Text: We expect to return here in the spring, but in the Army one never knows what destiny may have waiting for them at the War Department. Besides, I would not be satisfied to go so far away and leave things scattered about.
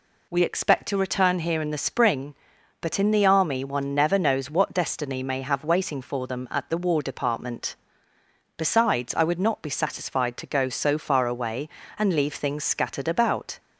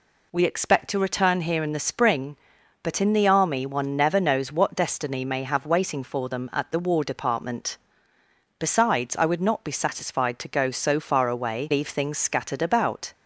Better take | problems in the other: first | skips "and"; at 11.7 s

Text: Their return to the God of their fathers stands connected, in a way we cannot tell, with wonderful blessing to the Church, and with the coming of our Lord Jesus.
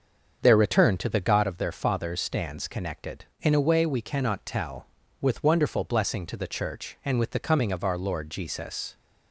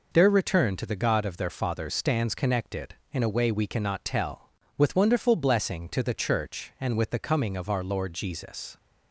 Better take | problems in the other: second | starts louder than the rest; until 1.5 s; 7 dB

